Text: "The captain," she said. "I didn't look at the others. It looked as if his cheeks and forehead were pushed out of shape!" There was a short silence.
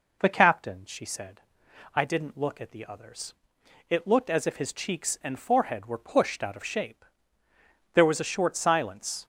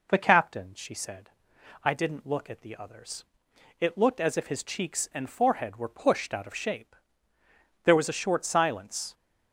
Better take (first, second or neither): neither